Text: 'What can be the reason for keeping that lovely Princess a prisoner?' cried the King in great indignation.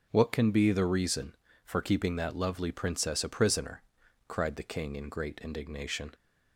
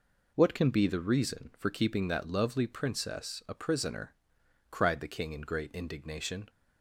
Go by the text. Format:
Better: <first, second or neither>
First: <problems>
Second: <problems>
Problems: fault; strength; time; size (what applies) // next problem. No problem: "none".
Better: neither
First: none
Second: none